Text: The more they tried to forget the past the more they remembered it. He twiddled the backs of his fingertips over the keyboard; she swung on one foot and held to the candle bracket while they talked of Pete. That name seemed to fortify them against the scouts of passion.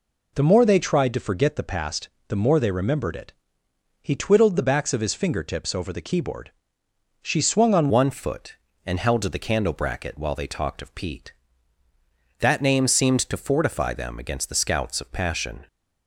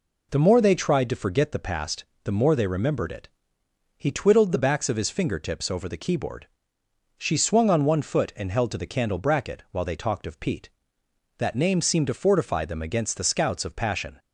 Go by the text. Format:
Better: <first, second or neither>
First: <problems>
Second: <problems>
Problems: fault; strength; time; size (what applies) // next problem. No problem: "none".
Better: second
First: pauses between "past" and "the"; slight; at 2.0 s; 0.20 s long // changes voice at "one"; from 7.8 s on; 7.8 s long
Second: pauses between "past" and "the"; slight; at 2.0 s; 0.20 s long